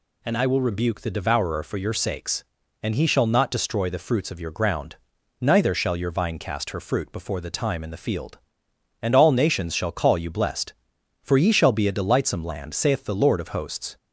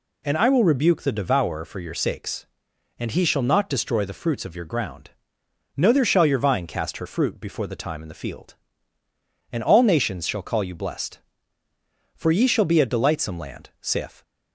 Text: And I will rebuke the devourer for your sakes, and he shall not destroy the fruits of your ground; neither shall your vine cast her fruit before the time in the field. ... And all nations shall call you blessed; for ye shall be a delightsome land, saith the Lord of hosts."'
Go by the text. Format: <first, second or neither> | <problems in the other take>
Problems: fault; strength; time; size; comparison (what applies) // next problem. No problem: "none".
first | stops before "the Lord of hosts"; at 14.2 s